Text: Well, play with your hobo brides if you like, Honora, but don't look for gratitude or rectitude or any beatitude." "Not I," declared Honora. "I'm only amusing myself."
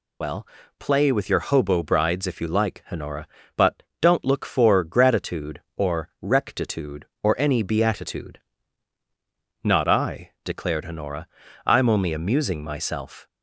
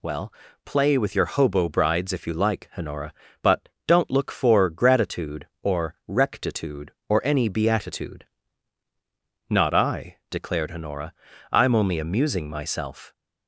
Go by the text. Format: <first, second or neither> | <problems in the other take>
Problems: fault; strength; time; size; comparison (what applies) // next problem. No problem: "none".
second | loses the start of "Well"; at 0.2 s; 45 ms // pauses between "but" and "don't"; slight; at 3.8 s; 0.18 s long; slight in the second